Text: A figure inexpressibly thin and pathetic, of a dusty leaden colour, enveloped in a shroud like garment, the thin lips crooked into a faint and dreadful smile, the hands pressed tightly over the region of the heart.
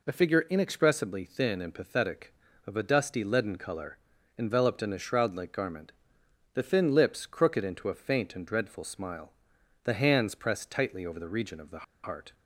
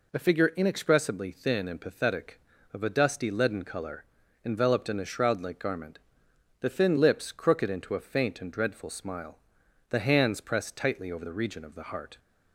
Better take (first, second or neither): second